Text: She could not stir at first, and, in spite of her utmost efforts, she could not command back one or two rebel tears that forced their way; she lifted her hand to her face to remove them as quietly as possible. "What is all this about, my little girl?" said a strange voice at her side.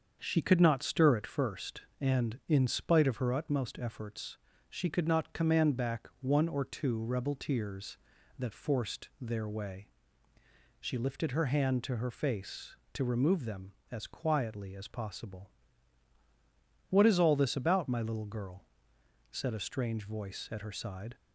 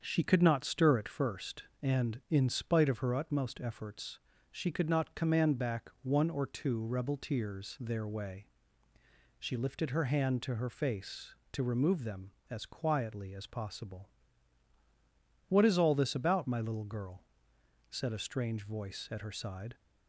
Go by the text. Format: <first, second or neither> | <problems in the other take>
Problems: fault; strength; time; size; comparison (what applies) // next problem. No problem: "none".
first | starts louder than the rest; strong; until 1.0 s; 7 dB; also in the first // skips "that forced"; at 7.7 s